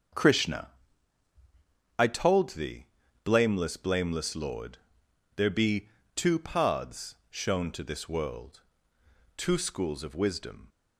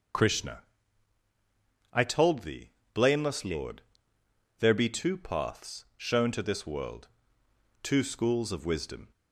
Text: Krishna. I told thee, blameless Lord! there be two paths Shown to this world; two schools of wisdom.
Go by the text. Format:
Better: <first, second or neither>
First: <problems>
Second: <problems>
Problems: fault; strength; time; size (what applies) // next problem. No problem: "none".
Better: second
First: starts louder than the rest; until 2.4 s; 7 dB // says "blameless" twice; at 3.7 s // pauses between "be" and "two"; slight; at 5.8 s; 0.26 s long // pauses between "paths" and "Shown"; slight; at 7.1 s; 0.16 s long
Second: none